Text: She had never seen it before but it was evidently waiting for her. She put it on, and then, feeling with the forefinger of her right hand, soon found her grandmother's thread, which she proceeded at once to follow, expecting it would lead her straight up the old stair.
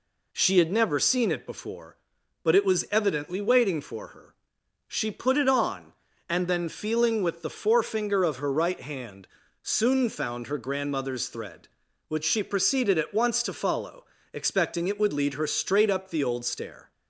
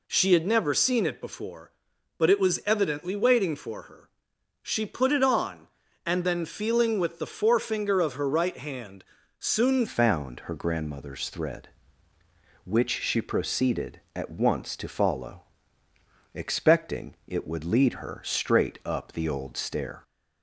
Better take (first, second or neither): first